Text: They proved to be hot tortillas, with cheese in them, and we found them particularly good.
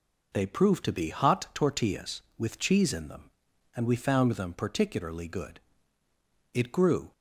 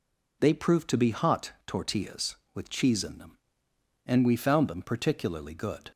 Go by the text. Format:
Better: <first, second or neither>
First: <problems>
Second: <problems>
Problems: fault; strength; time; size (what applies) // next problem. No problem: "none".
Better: second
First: goes on to say "It grew"; from 6.5 s on; 0.58 s long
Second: none